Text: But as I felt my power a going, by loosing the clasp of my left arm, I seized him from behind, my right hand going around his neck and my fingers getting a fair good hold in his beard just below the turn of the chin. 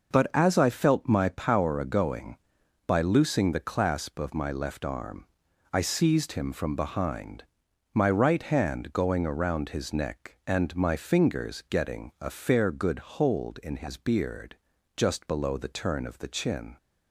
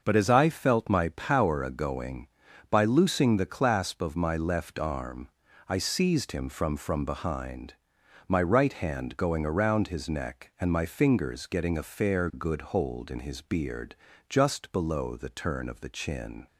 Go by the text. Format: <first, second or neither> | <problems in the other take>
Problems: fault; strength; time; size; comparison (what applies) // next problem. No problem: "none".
first | starts louder than the rest; until 1.0 s; 6 dB // says "from" twice; at 6.7 s // pauses between "beard" and "just"; slight; at 13.9 s; 0.32 s long; also in the first